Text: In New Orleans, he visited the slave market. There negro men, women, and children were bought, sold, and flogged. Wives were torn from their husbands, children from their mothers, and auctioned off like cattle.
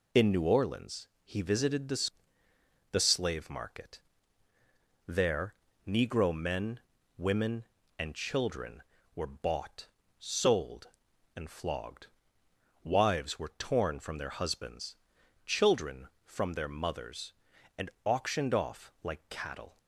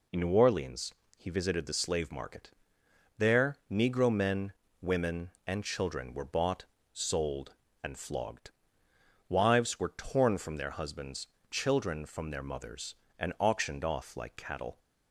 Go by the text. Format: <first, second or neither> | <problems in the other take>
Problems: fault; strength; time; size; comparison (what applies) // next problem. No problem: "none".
second | says "the" twice; at 2.9 s // pauses between "There" and "negro"; slight; at 5.5 s; 0.34 s long